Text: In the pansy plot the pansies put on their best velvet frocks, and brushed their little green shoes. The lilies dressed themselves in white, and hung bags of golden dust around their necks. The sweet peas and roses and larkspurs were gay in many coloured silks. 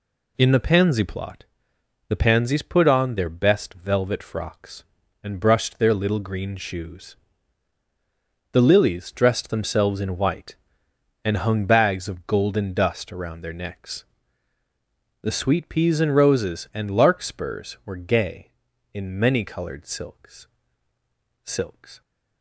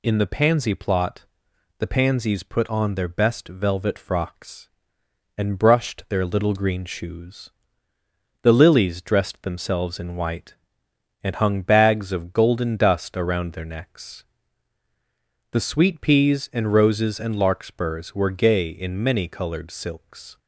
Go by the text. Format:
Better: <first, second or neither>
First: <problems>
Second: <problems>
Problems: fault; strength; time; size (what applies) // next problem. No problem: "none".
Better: second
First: pauses between "plot" and "the"; noticeable; at 1.4 s; 0.64 s long // says "silks" twice; at 21.4 s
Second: pauses between "plot" and "the"; noticeable; at 1.2 s; 0.52 s long